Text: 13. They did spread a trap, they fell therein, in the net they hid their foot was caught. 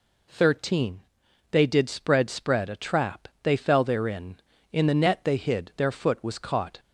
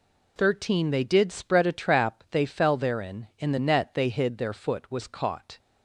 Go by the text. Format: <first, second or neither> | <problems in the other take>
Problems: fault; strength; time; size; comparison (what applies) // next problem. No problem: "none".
second | says "spread" twice; at 2.2 s